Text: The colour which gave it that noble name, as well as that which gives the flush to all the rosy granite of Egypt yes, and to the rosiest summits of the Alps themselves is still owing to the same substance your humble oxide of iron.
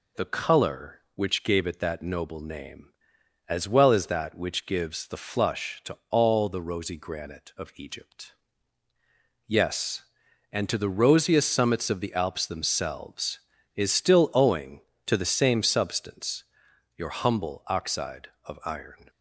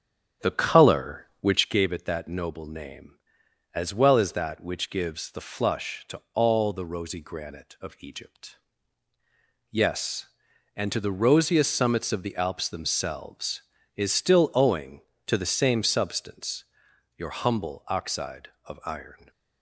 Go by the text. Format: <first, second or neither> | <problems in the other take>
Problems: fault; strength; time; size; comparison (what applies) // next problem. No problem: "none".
first | starts louder than the rest; strong; until 1.8 s; 8.5 dB // pauses between "Egypt" and "yes"; at 8.5 s; 1.1 s long; also in the first // pauses between "substance" and "your"; noticeable; at 16.6 s; 0.52 s long; noticeable in the first